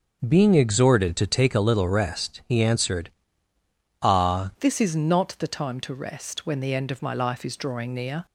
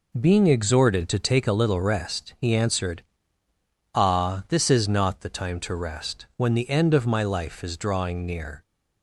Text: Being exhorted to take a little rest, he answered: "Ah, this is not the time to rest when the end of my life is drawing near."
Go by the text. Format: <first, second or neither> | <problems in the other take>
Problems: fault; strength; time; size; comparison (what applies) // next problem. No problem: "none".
second | changes voice at "this"; from 4.6 s on; 3.6 s long